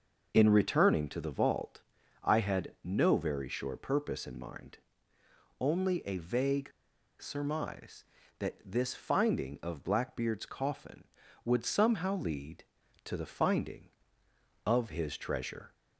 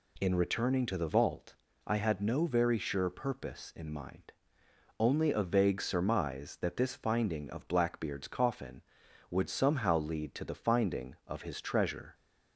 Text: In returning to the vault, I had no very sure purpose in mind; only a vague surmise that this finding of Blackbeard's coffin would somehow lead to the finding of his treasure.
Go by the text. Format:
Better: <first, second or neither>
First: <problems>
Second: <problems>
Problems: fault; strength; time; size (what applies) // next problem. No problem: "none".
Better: second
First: pauses between "vague" and "surmise"; noticeable; at 6.6 s; 0.50 s long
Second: none